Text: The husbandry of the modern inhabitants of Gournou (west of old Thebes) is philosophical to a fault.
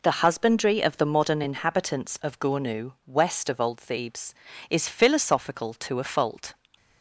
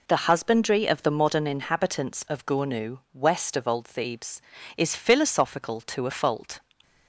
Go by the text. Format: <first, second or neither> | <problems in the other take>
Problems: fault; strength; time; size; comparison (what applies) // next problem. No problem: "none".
neither | none